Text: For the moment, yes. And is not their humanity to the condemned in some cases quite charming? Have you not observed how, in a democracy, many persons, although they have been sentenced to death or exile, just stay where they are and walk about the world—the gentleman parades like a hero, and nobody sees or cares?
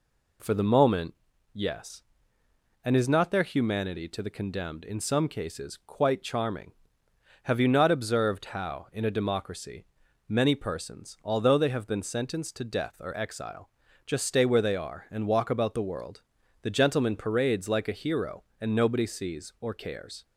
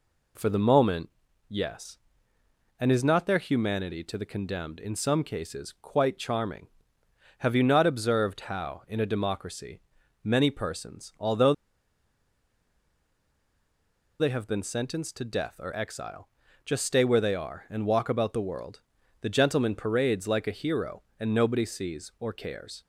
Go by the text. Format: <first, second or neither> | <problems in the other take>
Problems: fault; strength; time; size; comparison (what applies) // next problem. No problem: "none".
first | pauses between "although" and "they"; strong; at 11.5 s; 2.6 s long